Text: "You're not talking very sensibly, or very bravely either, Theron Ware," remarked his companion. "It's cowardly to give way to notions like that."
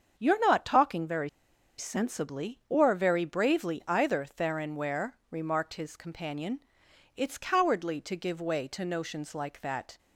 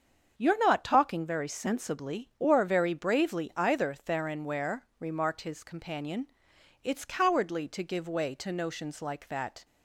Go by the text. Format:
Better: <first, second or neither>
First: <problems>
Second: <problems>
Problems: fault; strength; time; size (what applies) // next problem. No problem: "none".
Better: second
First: starts louder than the rest; strong; until 1.1 s; 7 dB // pauses between "very" and "sensibly"; noticeable; at 1.2 s; 0.49 s long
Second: starts louder than the rest; strong; until 1.3 s; 7 dB